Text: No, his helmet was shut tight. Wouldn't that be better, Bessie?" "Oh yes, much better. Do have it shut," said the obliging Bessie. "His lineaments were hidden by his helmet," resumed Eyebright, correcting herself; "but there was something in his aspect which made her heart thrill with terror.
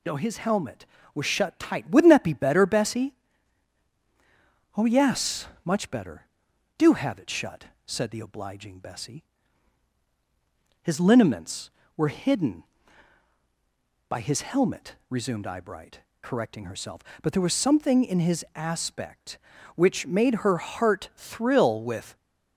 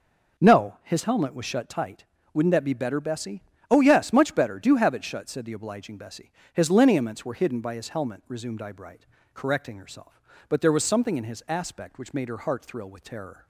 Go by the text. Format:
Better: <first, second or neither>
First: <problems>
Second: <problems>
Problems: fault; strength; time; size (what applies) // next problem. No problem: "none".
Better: second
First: stops before "terror"; at 22.1 s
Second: none